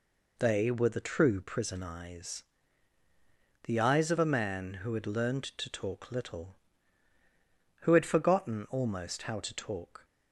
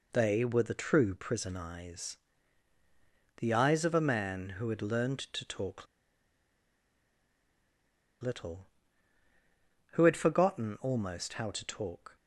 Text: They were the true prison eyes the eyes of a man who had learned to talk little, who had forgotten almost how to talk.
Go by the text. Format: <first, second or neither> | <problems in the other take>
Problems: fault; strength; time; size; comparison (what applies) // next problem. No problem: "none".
first | pauses between "eyes" and "the"; at 2.1 s; 1.2 s long; also in the first // pauses between "talk" and "little"; strong; at 5.8 s; 2.3 s long